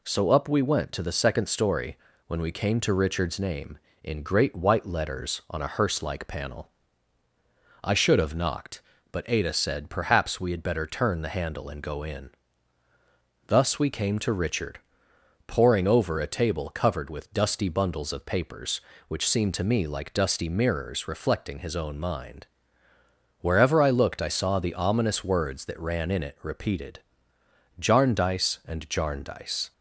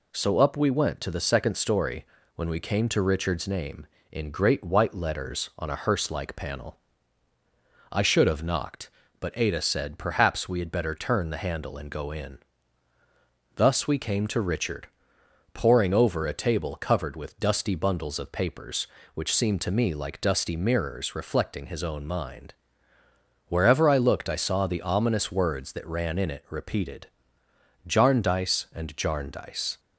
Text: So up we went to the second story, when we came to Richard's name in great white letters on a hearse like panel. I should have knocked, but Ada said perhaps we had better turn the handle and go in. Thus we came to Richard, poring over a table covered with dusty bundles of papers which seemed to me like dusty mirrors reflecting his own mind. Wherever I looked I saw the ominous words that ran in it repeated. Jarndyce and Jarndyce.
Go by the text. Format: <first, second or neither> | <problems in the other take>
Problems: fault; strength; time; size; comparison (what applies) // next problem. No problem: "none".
neither | none